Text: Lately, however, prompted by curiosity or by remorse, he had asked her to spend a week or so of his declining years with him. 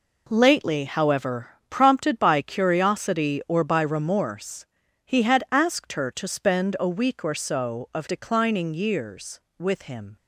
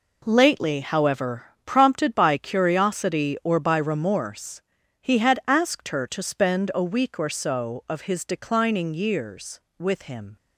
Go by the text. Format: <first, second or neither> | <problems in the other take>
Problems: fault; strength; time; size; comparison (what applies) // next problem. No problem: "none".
second | skips "his"; at 8.0 s